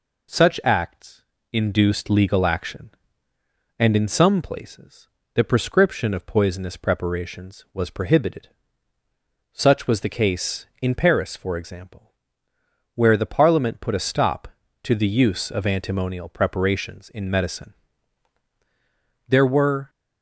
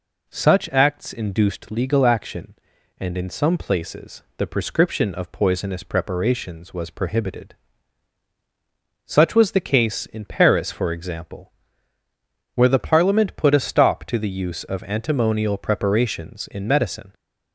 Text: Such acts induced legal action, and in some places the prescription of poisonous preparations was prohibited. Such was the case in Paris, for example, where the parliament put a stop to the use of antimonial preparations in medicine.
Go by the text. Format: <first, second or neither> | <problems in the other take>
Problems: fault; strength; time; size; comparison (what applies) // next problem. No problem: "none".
second | pauses between "acts" and "induced"; slight; at 1.2 s; 0.28 s long // pauses between "places" and "the"; slight; at 5.0 s; 0.26 s long // goes on to say "There were"; noticeable; from 19.2 s on; 0.62 s long